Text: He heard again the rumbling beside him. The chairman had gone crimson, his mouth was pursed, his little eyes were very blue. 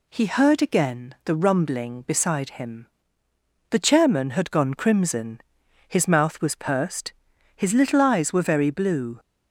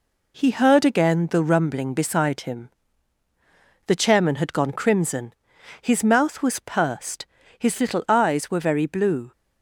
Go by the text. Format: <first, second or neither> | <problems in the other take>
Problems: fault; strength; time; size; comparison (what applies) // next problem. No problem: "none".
first | gets quieter; noticeable; throughout; 5 dB